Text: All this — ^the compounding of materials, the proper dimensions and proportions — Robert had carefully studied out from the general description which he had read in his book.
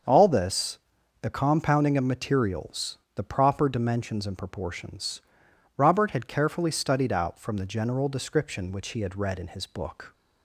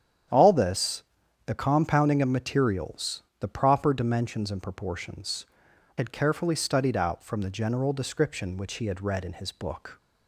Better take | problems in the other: first | starts louder than the rest; strong; until 1.7 s; 9 dB; also in the first // skips "Robert"; at 5.7 s

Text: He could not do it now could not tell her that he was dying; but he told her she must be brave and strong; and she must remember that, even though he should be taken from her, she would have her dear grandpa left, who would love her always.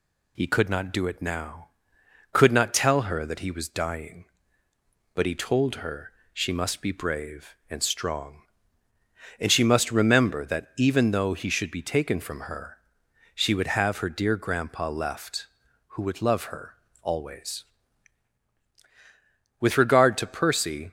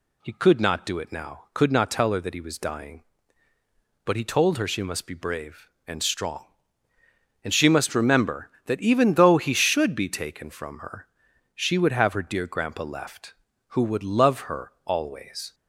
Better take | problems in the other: second | pauses between "her" and "she"; slight; at 6.1 s; 0.22 s long // pauses between "her" and "always"; slight; at 16.7 s; 0.26 s long // goes on to say "With regard to Percy"; from 19.5 s on; 1.3 s long

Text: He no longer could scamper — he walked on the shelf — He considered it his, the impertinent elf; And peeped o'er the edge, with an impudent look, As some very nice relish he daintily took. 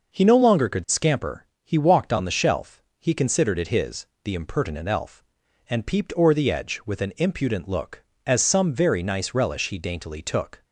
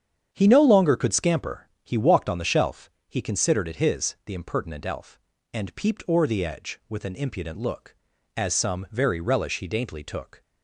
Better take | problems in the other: first | starts louder than the rest; strong; until 1.3 s; 8.5 dB // skips "nice"; at 9.1 s

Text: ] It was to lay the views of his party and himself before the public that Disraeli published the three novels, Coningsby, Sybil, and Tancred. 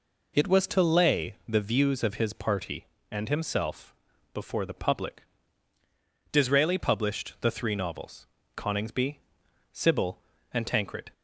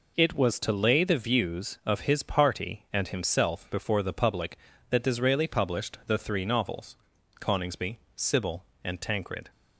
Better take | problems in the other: second | pauses between "himself" and "before"; at 3.9 s; 0.38 s long // skips "that"; at 5.7 s

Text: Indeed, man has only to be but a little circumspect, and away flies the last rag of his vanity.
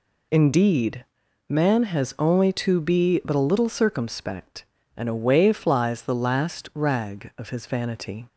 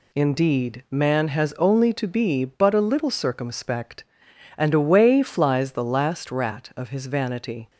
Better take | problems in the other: first | says "rat" for "rag"; at 6.2 s

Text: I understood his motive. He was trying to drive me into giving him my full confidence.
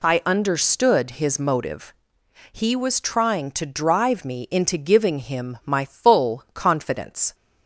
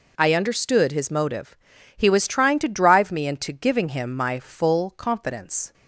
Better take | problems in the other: neither | none

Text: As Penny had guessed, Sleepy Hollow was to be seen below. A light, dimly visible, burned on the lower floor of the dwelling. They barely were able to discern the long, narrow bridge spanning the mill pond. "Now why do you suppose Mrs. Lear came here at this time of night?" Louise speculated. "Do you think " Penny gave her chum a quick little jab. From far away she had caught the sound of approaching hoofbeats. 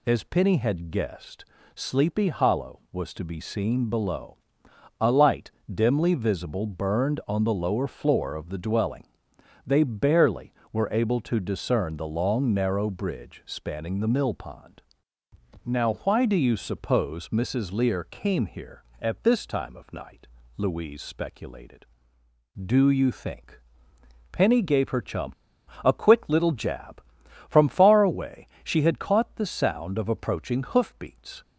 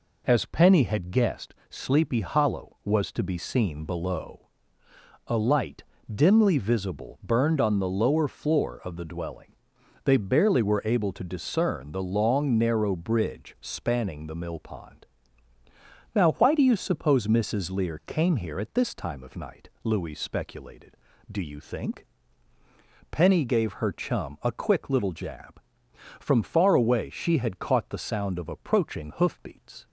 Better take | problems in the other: second | pauses between "chum" and "a"; noticeable; at 25.3 s; 0.51 s long // pauses between "away" and "she"; slight; at 28.4 s; 0.18 s long

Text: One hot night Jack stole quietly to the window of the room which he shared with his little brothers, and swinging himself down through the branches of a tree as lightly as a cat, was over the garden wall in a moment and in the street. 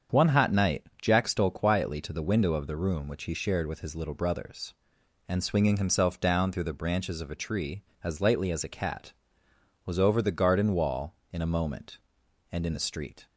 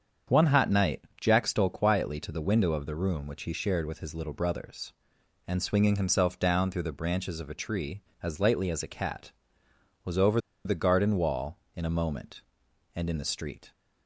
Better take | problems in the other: first | starts louder than the rest; strong; until 1.4 s; 7.5 dB; strong in the first // pauses between "night" and "Jack"; slight; at 1.0 s; 0.18 s long; slight in the first // pauses between "over" and "the"; slight; at 10.3 s; 0.26 s long

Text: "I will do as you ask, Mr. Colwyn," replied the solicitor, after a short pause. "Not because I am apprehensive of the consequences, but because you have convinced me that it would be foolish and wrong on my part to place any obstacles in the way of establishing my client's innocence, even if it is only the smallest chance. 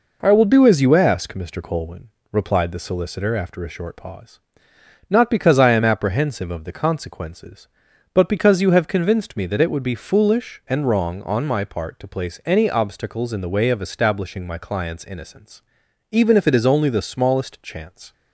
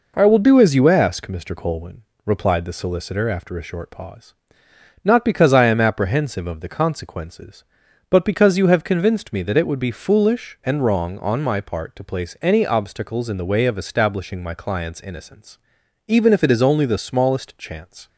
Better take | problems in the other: neither | none

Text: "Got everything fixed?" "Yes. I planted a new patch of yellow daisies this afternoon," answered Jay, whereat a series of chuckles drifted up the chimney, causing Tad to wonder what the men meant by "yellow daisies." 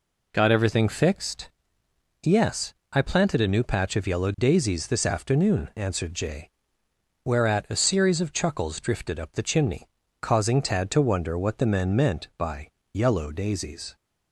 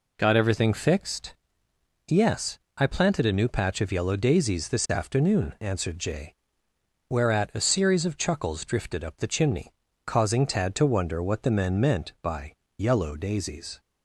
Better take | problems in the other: neither | pauses between "by" and "yellow"; slight; the same in both

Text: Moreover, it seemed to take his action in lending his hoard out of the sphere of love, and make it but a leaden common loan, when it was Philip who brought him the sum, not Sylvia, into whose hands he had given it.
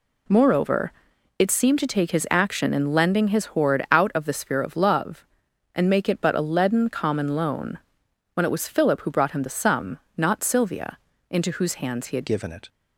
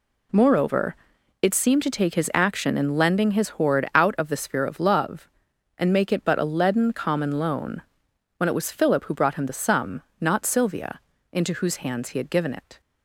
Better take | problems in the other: second | changes voice at "given"; from 12.2 s on; 0.4 s long

